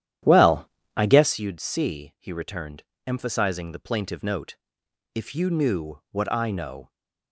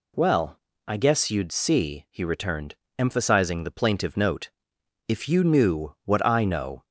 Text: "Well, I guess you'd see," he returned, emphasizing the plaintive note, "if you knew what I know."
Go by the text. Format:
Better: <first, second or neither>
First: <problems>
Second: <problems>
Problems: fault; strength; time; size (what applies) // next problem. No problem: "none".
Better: second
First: starts louder than the rest; strong; until 1.3 s; 11 dB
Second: none